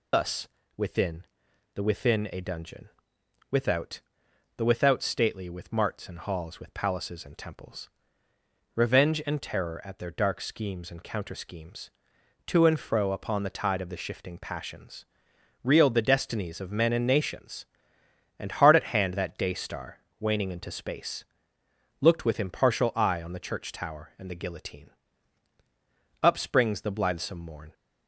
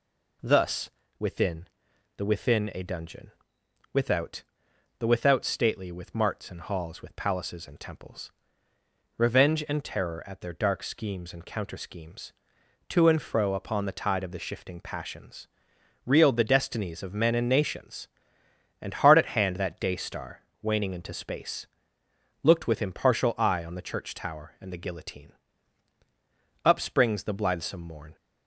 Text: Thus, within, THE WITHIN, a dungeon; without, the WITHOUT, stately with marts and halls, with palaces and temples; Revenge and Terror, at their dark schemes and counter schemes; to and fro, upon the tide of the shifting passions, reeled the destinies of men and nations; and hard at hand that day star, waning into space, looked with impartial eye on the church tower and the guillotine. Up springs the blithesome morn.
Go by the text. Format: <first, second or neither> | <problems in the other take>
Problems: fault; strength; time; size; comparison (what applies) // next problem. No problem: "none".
second | loses the start of "Thus"; at 0.1 s; 140 ms